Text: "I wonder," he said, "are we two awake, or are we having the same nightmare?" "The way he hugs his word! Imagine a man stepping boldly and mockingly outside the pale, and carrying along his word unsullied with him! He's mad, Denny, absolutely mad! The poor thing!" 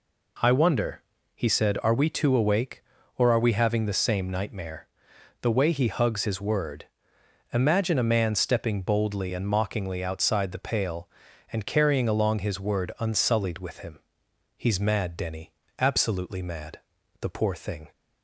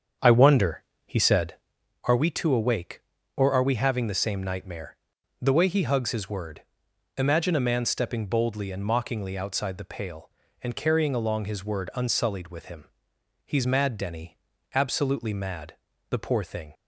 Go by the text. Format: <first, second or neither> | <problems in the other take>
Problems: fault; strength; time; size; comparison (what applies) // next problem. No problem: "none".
first | starts louder than the rest; strong; until 1.9 s; 7.5 dB